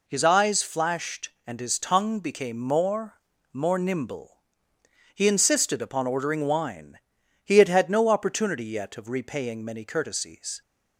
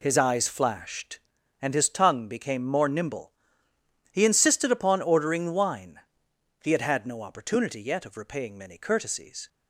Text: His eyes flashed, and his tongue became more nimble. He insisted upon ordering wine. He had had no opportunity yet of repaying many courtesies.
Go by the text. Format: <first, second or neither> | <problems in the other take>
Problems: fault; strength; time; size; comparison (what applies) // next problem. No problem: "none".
second | says "more" twice; at 3.5 s